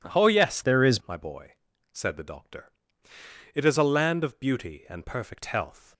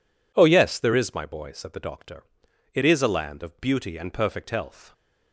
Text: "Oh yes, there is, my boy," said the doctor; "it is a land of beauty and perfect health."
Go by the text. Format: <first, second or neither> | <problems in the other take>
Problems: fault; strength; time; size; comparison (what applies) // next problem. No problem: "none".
second | changes voice from "there" to "is"; from 0.6 to 1.0 s; 0.4 s long